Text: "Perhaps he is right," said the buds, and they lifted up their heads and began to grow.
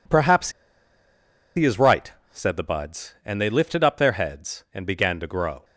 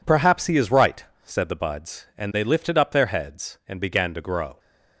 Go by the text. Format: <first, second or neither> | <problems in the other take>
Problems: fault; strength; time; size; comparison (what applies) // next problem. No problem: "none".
second | pauses between "Perhaps" and "he"; at 0.5 s; 1.0 s long